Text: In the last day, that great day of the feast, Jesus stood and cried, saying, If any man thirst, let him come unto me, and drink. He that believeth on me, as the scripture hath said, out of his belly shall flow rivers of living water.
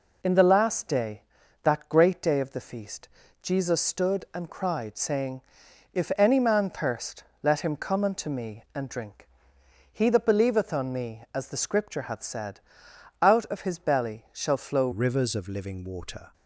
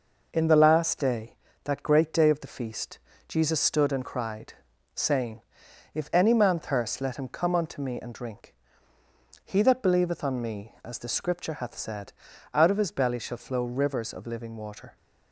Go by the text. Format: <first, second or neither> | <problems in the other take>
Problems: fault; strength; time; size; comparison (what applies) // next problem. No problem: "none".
second | changes voice at "rivers"; from 14.9 s on; 1.4 s long